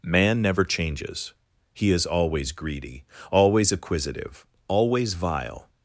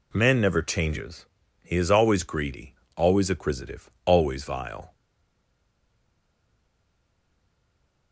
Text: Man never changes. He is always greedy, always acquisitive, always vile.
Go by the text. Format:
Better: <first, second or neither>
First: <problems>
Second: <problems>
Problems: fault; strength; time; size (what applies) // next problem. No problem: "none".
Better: first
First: none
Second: stays silent after the last word; strong; from 4.9 s on; 3.2 s long